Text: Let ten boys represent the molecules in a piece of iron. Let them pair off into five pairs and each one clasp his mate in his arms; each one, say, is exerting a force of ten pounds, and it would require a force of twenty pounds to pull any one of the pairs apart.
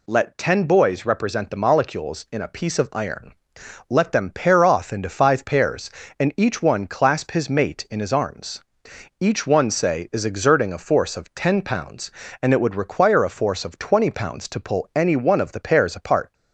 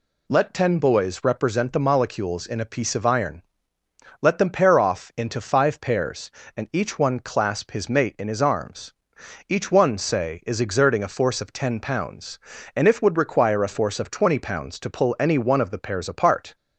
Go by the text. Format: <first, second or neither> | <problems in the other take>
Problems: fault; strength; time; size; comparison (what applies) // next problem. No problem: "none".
first | says "if" for "it"; at 12.8 s